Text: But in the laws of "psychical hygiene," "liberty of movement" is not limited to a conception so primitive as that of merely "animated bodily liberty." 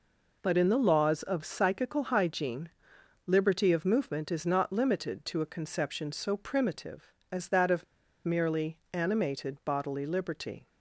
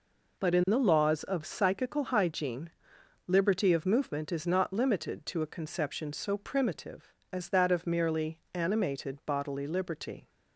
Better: second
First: pauses between "of" and "merely"; at 7.8 s; 0.40 s long // pauses between "merely" and "animated"; slight; at 8.7 s; 0.16 s long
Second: pauses between "merely" and "animated"; slight; at 8.3 s; 0.16 s long

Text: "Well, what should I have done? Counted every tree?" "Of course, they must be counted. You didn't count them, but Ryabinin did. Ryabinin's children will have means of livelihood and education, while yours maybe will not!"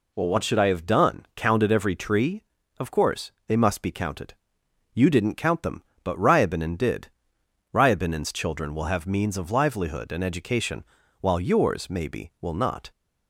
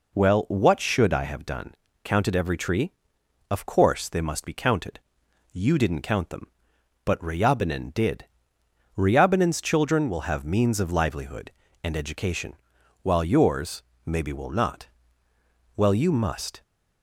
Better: first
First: none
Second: pauses between "yours" and "maybe"; slight; at 13.8 s; 0.24 s long // goes on to say "Well you must"; noticeable; from 15.7 s on; 0.86 s long

